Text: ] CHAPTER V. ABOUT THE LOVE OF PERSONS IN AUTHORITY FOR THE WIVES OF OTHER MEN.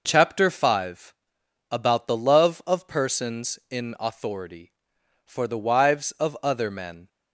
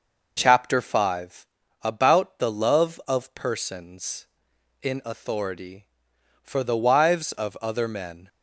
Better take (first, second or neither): neither